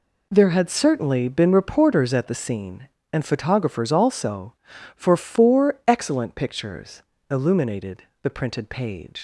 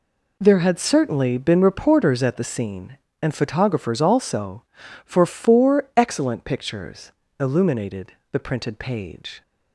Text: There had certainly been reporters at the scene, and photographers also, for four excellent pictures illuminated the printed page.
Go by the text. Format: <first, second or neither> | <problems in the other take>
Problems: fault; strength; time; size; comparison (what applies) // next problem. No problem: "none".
second | pauses between "pictures" and "illuminated"; slight; at 7.0 s; 0.28 s long; slight in the second // pauses between "illuminated" and "the"; slight; at 8.0 s; 0.18 s long; slight in the second // leaves "page" unfinished; at 9.1 s; 90 ms